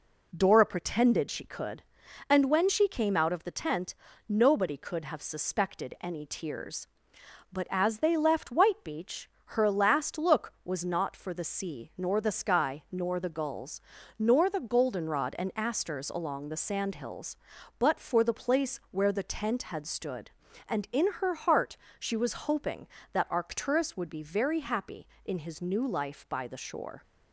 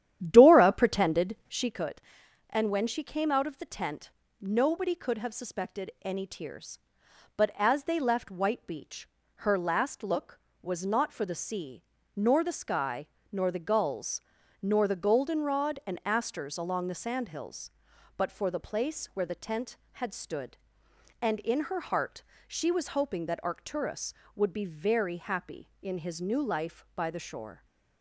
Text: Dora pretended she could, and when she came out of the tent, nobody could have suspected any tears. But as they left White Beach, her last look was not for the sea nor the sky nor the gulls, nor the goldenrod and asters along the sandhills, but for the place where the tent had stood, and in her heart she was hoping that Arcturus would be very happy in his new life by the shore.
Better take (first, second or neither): first